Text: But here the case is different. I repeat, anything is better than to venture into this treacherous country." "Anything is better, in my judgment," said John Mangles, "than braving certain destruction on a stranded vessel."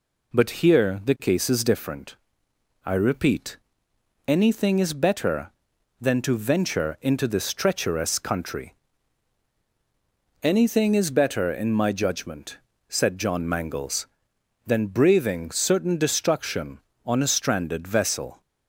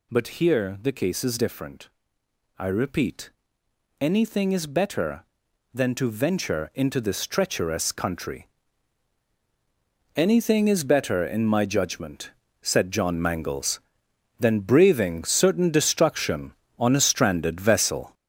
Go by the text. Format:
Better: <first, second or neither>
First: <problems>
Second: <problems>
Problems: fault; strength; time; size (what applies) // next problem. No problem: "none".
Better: first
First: none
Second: gets louder; throughout; 6.5 dB